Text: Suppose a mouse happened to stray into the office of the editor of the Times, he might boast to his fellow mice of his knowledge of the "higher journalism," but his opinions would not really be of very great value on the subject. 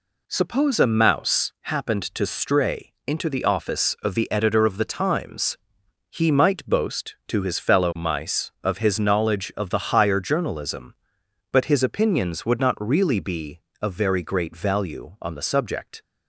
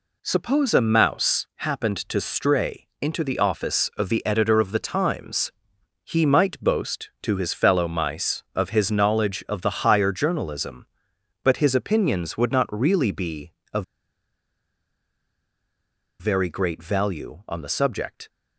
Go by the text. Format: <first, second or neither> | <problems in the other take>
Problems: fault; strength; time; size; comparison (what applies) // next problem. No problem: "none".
first | pauses between "of" and "very"; strong; at 13.8 s; 2.3 s long